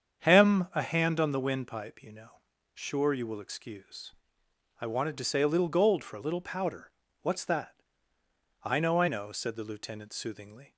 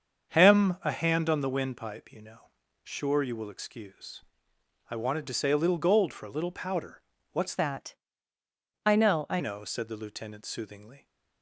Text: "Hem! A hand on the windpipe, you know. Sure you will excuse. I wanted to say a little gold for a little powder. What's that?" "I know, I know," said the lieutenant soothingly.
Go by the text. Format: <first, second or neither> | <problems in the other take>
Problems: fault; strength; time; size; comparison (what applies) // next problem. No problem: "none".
first | starts louder than the rest; until 1.4 s; 7 dB; strong in the first // changes voice from "that" to "I"; from 7.5 to 9.3 s; 1.8 s long